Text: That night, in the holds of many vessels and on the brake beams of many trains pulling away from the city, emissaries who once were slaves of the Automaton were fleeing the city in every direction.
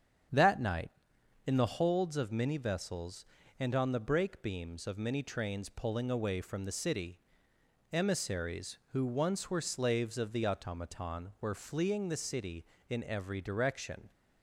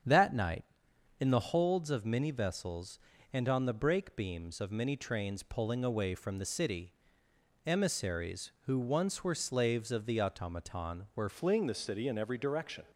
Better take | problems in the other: first | starts louder than the rest; strong; until 1.6 s; 8 dB; strong in the first // changes voice at "fleeing"; from 11.2 s on; 1.6 s long

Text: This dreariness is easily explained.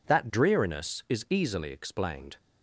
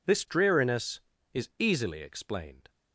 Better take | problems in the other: second | says "That" for "This"; at 0.0 s

